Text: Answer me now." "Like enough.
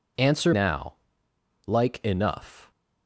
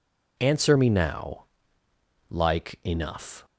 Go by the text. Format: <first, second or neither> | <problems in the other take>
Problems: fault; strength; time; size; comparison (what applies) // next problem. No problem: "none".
second | skips "me"; at 0.5 s